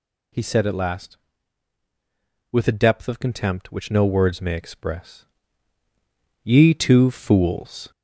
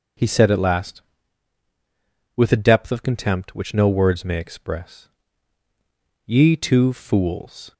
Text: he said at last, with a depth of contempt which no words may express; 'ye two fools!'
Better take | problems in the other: second | gets louder; slight; throughout; 2 dB

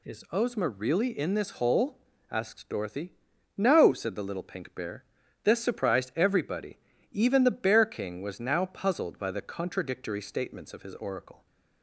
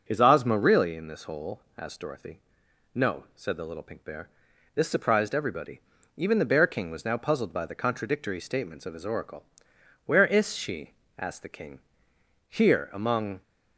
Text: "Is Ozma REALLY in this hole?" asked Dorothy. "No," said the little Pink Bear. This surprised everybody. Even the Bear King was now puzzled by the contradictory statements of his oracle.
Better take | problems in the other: first | goes on to say "Where IS she asked the King Here among"; strong; from 10.0 s on; 3.3 s long

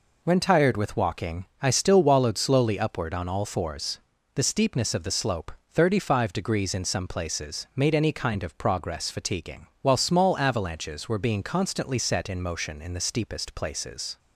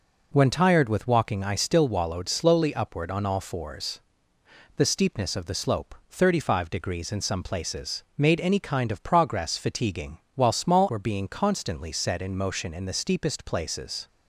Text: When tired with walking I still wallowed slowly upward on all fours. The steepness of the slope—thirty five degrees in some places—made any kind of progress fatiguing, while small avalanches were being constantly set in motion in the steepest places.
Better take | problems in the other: first | skips "avalanches"; at 10.8 s

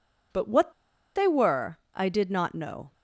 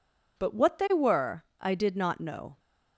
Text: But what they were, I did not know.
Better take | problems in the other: second | pauses between "what" and "they"; at 0.7 s; 0.45 s long

